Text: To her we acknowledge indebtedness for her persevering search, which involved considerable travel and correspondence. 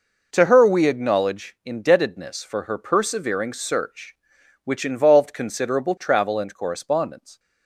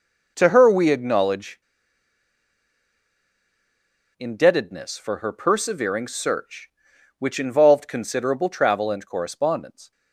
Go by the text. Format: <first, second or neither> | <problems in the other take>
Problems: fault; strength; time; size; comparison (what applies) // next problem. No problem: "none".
first | pauses between "acknowledge" and "indebtedness"; strong; at 1.6 s; 2.5 s long